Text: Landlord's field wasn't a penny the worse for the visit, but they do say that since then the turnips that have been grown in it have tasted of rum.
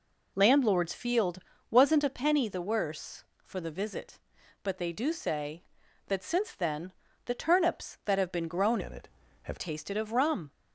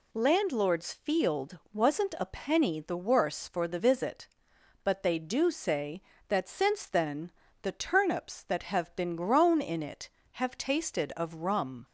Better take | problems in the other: second | pauses between "field" and "wasn't"; slight; at 1.3 s; 0.32 s long; slight in the second // pauses between "then" and "the"; slight; at 6.9 s; 0.32 s long; slight in the second // changes voice from "in" to "have"; from 8.8 to 9.5 s; 0.7 s long

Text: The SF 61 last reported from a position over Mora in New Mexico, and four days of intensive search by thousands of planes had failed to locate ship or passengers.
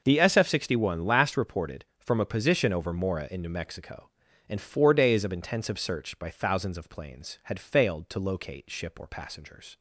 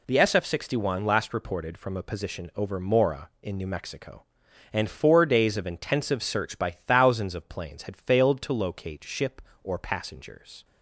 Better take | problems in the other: neither | none

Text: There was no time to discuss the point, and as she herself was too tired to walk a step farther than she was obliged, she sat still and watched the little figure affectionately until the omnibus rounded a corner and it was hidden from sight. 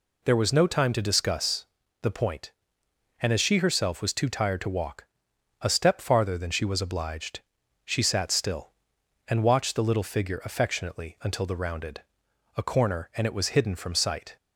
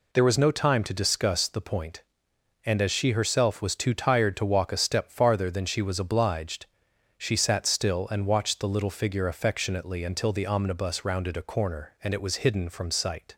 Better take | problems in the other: second | pauses between "discuss" and "the"; slight; at 1.6 s; 0.36 s long // pauses between "walk" and "a"; noticeable; at 5.0 s; 0.56 s long // skips "omnibus"; at 11.5 s // pauses between "rounded" and "a"; noticeable; at 12.0 s; 0.54 s long

